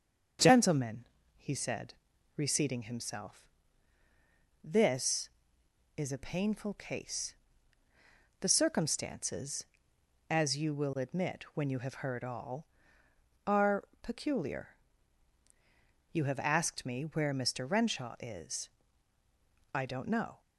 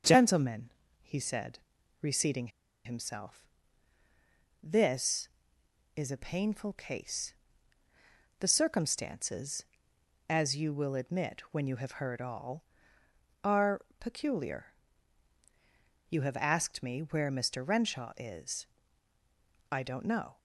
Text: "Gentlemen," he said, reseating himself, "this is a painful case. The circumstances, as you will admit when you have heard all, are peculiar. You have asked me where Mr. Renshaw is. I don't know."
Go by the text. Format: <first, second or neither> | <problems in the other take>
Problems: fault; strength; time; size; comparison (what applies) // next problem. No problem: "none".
first | starts louder than the rest; until 1.3 s; 6.5 dB; also in the first // pauses between "reseating" and "himself"; slight; at 2.4 s; 0.36 s long // pauses between "are" and "peculiar"; slight; at 13.8 s; 0.16 s long; slight in the first